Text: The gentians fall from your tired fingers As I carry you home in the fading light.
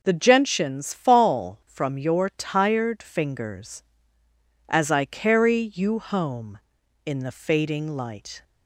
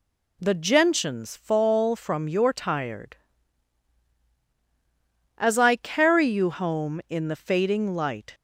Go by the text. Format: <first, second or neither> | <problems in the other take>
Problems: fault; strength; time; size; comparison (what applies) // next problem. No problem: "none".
first | skips "fingers"; at 4.2 s